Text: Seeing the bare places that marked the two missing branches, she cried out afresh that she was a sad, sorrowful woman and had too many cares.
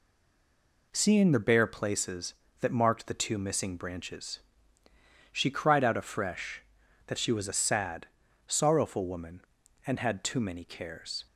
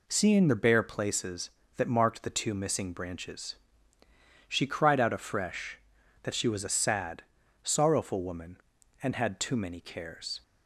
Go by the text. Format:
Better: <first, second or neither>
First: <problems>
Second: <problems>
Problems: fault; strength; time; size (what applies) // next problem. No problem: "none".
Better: second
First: stays silent before the first word; slight; until 0.9 s; 0.9 s long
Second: none